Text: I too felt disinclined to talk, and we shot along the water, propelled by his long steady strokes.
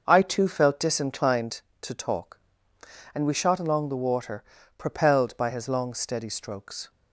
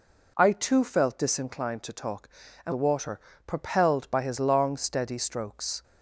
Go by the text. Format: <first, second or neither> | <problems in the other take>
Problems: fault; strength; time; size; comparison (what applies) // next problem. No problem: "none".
first | skips "we shot along"; at 2.7 s